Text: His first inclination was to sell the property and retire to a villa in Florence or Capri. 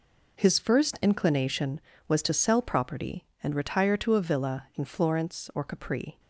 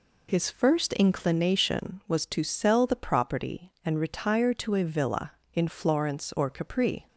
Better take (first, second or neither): second